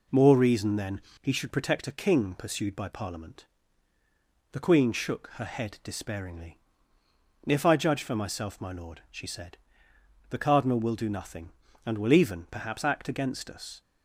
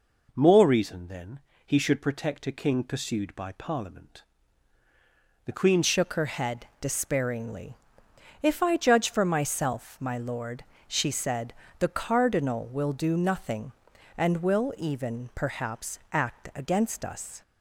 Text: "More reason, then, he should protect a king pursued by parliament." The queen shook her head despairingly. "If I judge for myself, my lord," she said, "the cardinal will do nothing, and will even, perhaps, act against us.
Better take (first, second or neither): first